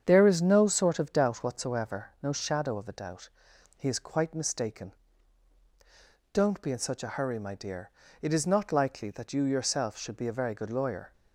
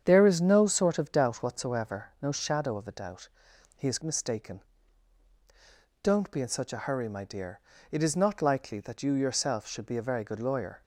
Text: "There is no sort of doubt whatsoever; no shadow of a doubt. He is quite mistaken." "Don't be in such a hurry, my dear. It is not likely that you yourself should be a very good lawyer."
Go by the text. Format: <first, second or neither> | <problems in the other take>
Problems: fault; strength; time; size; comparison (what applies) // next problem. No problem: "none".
first | starts louder than the rest; strong; until 1.0 s; 8 dB; strong in the first // skips "quite"; at 4.0 s